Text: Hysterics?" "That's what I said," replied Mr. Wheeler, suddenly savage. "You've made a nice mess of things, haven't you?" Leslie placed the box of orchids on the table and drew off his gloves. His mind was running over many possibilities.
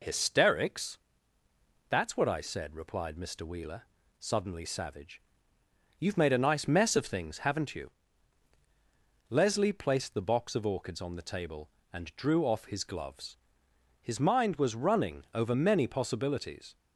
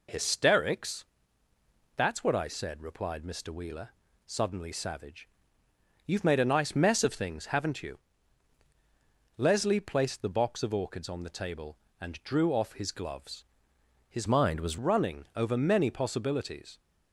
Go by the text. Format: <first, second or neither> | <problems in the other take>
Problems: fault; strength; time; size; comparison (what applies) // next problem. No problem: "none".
first | changes voice from "mind" to "was"; from 14.2 to 14.7 s; 0.5 s long